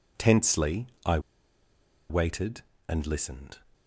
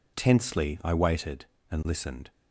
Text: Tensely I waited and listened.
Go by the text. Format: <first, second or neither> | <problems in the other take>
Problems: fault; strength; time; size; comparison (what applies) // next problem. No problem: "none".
second | pauses between "Tensely" and "I"; slight; at 0.8 s; 0.18 s long // pauses between "I" and "waited"; noticeable; at 1.1 s; 0.90 s long